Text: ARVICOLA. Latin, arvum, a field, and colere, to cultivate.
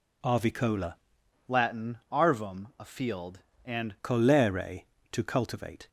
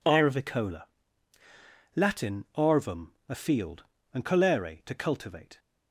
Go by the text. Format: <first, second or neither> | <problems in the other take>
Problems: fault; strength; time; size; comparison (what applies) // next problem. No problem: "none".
second | changes voice from "Latin" to "and"; from 1.4 to 3.9 s; 2.5 s long